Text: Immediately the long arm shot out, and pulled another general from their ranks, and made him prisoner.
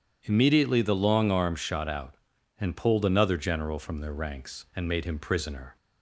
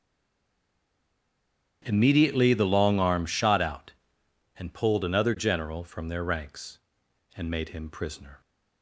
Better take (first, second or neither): first